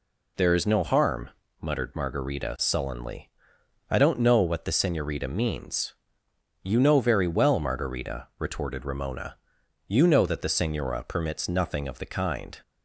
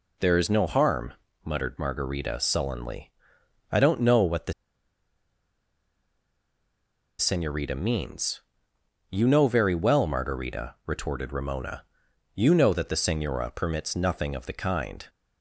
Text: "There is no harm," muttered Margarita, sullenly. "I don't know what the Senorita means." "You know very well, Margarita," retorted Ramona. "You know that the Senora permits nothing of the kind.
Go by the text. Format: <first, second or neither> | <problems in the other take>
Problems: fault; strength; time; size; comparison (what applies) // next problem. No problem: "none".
first | pauses between "the" and "Senorita"; strong; at 4.5 s; 2.6 s long